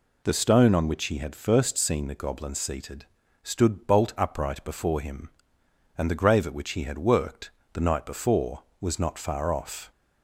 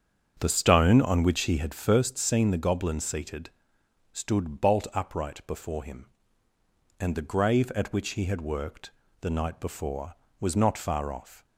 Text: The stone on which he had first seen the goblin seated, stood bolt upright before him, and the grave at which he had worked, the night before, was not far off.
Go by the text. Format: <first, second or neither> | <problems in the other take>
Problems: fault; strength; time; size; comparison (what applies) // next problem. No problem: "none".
first | starts louder than the rest; strong; until 2.1 s; 7.5 dB